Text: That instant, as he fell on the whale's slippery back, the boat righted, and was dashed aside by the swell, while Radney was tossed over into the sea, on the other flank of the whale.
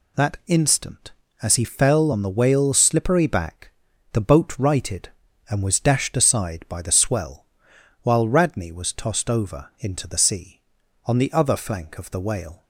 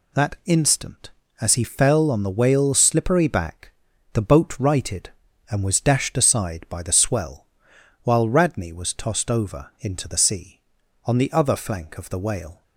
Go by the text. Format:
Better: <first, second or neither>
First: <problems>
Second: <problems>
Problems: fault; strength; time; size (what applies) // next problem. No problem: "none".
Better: neither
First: none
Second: none